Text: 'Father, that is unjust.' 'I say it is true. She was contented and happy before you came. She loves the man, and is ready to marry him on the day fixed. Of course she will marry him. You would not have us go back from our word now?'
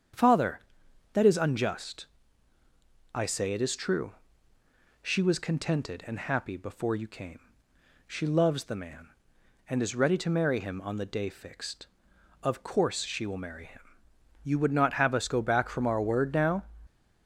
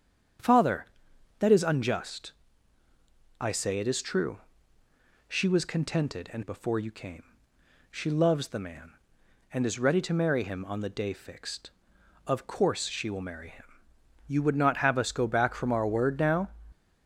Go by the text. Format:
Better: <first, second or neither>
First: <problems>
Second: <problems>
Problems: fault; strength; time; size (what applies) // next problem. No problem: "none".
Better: first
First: starts louder than the rest; strong; until 1.6 s; 7.5 dB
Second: starts louder than the rest; strong; until 1.9 s; 7.5 dB // skips "happy"; at 6.4 s